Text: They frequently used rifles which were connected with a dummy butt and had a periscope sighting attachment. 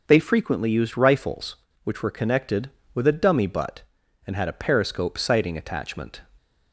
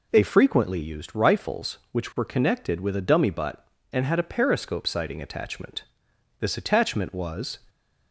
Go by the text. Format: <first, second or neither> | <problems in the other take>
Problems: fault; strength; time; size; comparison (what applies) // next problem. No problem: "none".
first | goes on to say "This attachment was"; noticeable; from 6.3 s on; 1.2 s long // stays silent after the last word; slight; from 7.5 s on; 0.6 s long; slight in the first